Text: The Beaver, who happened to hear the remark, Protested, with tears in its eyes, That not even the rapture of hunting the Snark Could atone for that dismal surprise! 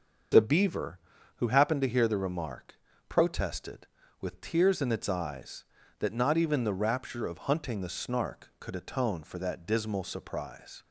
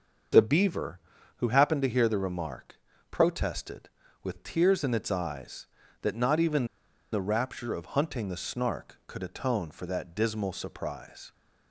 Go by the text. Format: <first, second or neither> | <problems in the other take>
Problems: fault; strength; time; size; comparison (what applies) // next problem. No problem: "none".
first | starts louder than the rest; until 1.7 s; 6.5 dB; also in the first // pauses between "even" and "the"; noticeable; at 6.6 s; 0.47 s long